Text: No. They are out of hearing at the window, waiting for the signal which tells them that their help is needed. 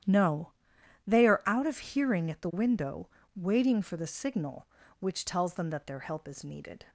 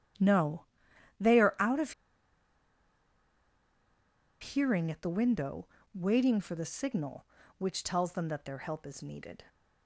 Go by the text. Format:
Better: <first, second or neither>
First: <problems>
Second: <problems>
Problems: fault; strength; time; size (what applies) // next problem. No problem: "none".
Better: first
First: starts louder than the rest; strong; until 1.6 s; 11 dB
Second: starts louder than the rest; strong; until 1.8 s; 11 dB // pauses between "of" and "hearing"; strong; at 1.9 s; 2.4 s long